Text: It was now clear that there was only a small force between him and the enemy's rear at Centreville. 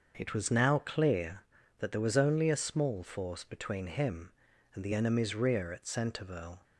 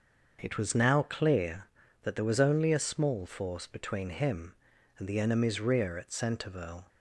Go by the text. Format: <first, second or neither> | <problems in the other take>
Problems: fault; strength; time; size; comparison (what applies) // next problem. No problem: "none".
neither | starts louder than the rest; the same in both